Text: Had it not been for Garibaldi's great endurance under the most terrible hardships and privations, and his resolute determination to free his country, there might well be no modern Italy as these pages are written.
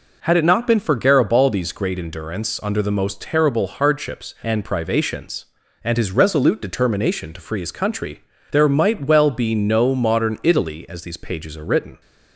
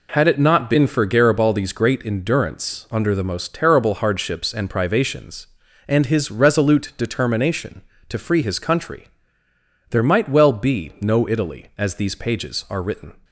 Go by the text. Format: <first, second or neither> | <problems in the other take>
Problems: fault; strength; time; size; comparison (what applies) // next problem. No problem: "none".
first | skips "modern"; at 11.2 s